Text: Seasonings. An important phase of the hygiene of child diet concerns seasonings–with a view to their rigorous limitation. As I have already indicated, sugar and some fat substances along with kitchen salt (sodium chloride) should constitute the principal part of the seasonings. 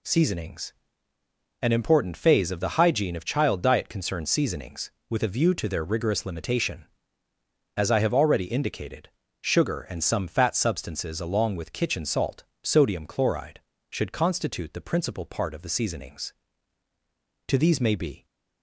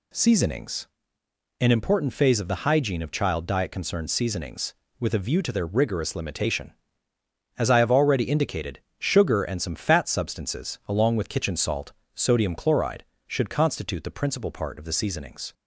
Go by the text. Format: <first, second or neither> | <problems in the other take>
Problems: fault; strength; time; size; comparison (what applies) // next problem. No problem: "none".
second | goes on to say "To these may be"; noticeable; from 17.4 s on; 0.78 s long